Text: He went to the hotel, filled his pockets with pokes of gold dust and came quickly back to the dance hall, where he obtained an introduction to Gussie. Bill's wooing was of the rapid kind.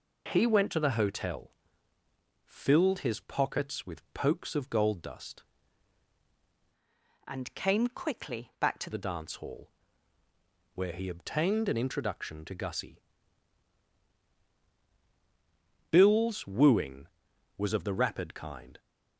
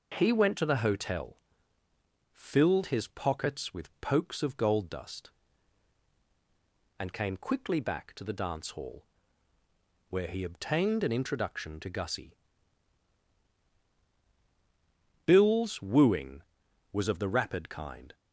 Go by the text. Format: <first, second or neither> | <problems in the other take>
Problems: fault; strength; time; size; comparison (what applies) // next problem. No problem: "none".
second | changes voice from "and" to "to"; from 7.2 to 8.9 s; 1.7 s long